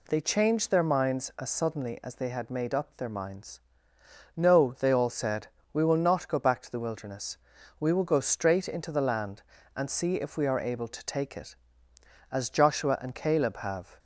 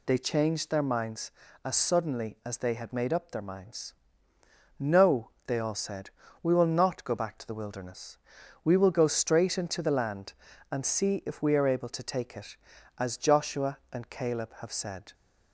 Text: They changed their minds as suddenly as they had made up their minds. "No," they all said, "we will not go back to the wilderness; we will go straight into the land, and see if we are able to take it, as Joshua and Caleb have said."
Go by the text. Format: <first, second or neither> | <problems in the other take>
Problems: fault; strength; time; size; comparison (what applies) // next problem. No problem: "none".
second | stops before "said"; at 13.9 s